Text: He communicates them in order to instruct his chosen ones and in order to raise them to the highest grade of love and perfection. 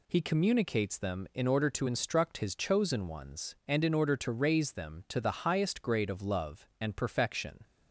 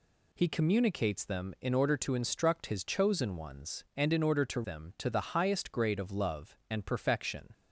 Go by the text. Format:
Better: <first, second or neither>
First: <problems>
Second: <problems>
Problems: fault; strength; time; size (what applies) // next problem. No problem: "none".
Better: first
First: none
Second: skips "raise"; at 4.6 s